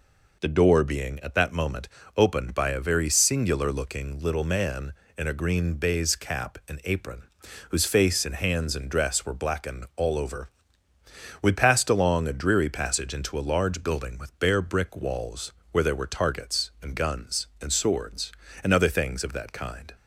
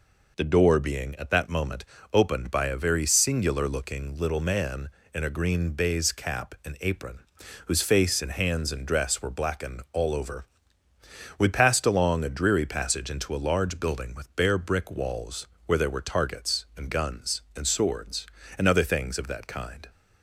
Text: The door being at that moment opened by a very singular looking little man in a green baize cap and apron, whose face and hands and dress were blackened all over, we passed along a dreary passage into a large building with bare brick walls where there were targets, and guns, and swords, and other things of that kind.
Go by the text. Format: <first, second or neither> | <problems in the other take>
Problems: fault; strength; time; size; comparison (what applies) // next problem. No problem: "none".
neither | pauses between "moment" and "opened"; slight; the same in both // pauses between "walls" and "where"; slight; the same in both